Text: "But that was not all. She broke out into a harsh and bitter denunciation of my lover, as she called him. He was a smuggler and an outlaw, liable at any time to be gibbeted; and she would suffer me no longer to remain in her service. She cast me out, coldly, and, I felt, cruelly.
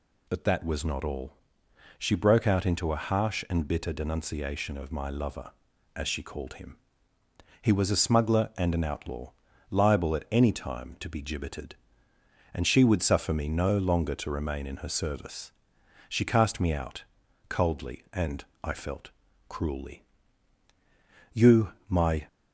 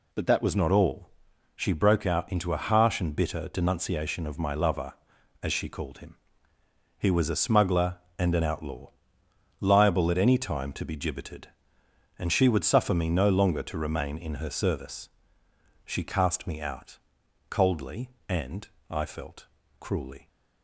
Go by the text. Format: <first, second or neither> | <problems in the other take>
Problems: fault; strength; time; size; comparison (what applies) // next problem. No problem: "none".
second | goes on to say "You my"; noticeable; from 21.3 s on; 0.94 s long